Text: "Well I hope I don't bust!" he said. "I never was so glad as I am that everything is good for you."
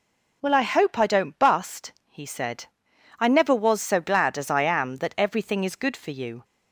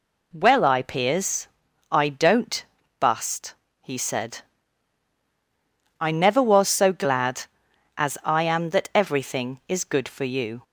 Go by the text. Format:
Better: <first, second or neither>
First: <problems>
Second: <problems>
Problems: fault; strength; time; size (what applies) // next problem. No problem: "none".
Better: first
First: none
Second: says "peers" for "hope"; at 0.8 s // pauses between "don't" and "bust"; at 2.6 s; 0.38 s long